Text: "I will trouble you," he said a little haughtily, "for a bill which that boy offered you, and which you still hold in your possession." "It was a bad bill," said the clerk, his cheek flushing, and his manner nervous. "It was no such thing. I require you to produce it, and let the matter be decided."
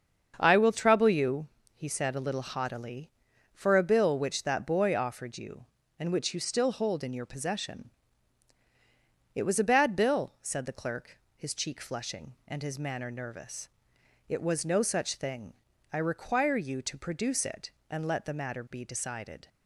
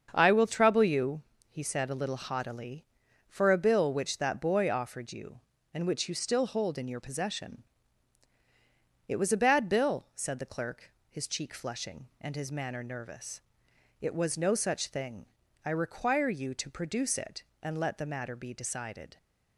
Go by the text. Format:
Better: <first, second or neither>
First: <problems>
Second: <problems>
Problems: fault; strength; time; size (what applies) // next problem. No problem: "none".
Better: neither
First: starts louder than the rest; until 1.3 s; 7 dB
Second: starts louder than the rest; until 1.1 s; 7 dB